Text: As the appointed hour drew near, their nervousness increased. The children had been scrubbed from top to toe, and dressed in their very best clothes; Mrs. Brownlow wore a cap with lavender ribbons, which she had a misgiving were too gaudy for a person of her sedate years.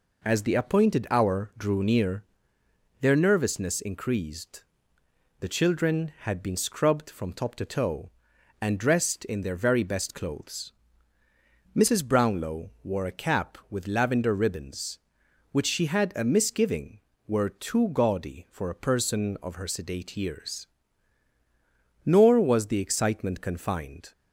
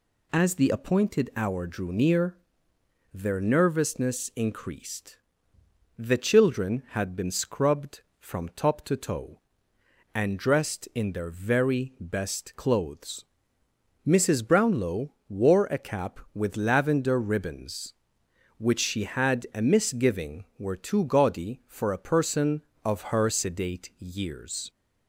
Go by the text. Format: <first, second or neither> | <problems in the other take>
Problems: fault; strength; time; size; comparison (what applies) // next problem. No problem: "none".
second | goes on to say "Nor was the excitement confined"; strong; from 22.0 s on; 2.0 s long